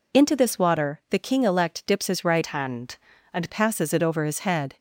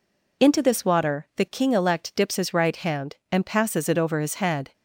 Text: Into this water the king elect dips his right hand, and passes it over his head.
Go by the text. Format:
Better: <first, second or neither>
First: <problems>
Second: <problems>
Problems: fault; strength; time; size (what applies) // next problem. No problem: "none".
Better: second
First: changes voice from "hand" to "and"; from 2.4 to 3.4 s; 1.0 s long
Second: none